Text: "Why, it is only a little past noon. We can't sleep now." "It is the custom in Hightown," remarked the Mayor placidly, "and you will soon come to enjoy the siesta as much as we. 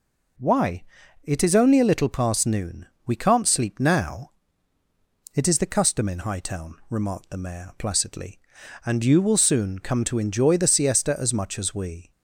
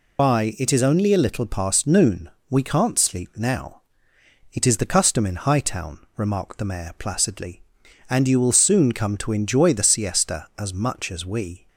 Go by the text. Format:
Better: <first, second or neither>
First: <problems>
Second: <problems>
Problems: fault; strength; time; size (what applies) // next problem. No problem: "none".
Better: first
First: none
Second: loses the start of "Why"; at 0.1 s; 80 ms